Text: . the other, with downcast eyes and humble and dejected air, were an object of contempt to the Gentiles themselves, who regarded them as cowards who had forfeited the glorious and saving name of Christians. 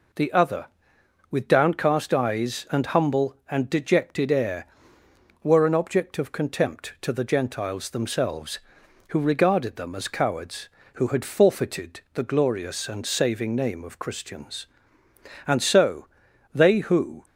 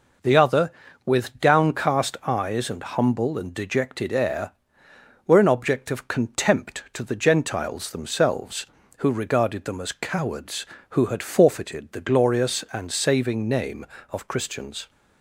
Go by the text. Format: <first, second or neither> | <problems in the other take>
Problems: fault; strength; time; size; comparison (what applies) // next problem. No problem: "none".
second | goes on to say "And so they who"; strong; from 15.4 s on; 1.7 s long